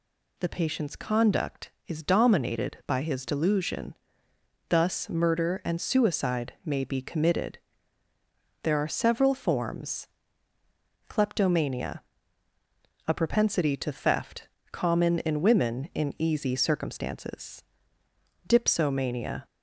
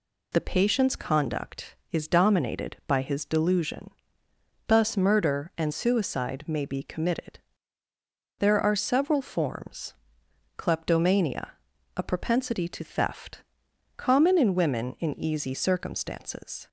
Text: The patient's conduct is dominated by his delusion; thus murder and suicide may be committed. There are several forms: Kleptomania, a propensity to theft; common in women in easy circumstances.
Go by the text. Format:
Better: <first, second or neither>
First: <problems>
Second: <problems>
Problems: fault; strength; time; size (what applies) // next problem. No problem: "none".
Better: second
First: goes on to say "Dipsomania"; noticeable; from 18.4 s on; 1.0 s long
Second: none